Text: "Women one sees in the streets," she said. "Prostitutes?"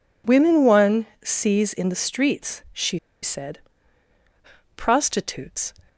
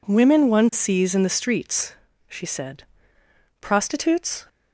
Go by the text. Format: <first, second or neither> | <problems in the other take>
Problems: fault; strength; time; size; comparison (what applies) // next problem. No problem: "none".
second | pauses between "one" and "sees"; slight; at 1.0 s; 0.18 s long // pauses between "she" and "said"; slight; at 2.9 s; 0.25 s long